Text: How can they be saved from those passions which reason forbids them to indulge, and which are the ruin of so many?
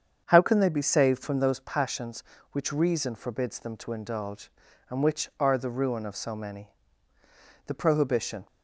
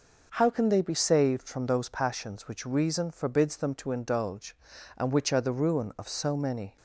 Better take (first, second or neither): second